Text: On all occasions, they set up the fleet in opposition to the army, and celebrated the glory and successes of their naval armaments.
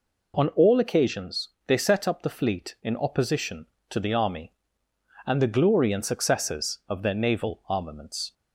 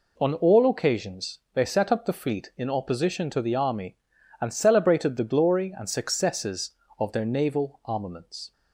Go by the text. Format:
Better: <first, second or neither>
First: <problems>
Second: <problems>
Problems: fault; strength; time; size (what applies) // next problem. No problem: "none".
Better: second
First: skips "celebrated"; at 5.4 s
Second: none